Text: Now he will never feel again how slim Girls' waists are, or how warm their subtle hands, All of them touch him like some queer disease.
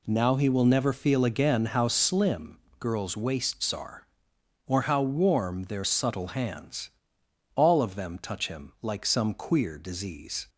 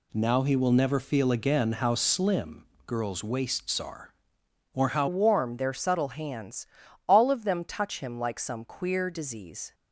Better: first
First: pauses between "slim" and "Girls"; slight; at 2.5 s; 0.20 s long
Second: pauses between "slim" and "Girls"; slight; at 2.6 s; 0.20 s long // changes voice at "warm"; from 5.0 s on; 4.7 s long

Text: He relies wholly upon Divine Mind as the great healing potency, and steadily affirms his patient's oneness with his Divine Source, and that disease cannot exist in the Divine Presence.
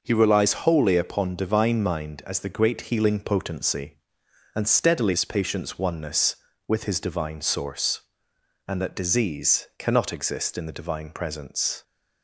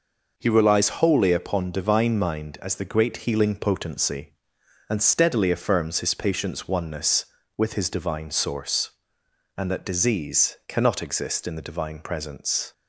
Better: second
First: skips "affirms"; at 5.1 s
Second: none

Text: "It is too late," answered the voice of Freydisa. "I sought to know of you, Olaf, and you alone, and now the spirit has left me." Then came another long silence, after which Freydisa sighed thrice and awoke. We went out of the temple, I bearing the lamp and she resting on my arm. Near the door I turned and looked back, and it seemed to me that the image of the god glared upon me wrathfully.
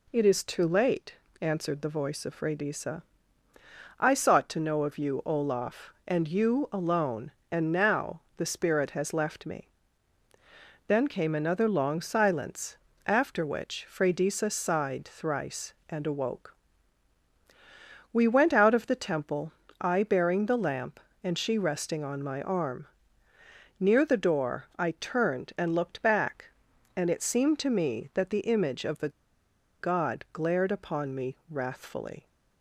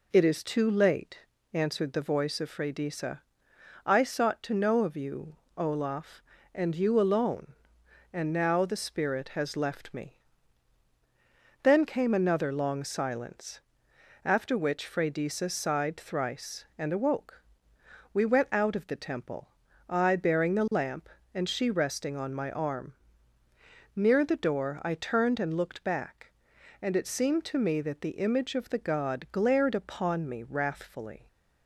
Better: second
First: pauses between "now" and "the"; slight; at 8.2 s; 0.16 s long // pauses between "the" and "god"; noticeable; at 29.0 s; 0.71 s long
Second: none

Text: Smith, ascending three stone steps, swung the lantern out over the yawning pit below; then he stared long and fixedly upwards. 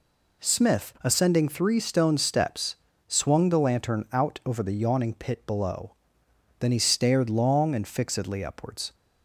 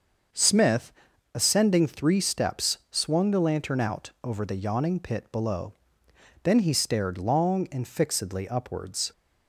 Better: first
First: none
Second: starts louder than the rest; until 1.7 s; 6.5 dB // skips "stone"; at 2.2 s

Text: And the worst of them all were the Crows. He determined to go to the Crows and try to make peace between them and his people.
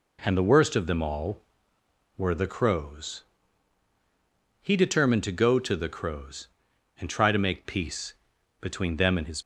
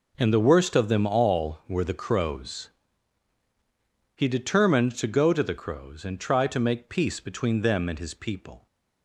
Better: second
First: pauses between "peace" and "between"; noticeable; at 8.1 s; 0.46 s long // stops before "people"; at 9.4 s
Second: none

